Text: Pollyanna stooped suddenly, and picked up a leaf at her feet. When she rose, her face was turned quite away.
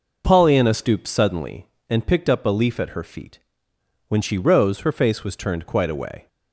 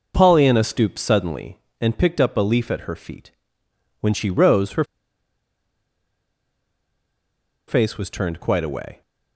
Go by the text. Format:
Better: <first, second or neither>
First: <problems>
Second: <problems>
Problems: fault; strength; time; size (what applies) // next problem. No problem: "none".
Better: first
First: none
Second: pauses between "her" and "face"; strong; at 4.8 s; 2.8 s long